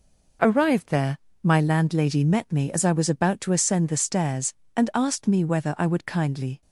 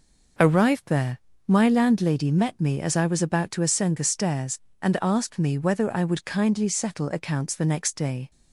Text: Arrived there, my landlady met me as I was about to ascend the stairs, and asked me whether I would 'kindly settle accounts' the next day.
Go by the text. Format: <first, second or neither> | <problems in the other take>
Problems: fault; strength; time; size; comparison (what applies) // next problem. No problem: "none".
second | stops before "settle accounts the next day"; at 6.6 s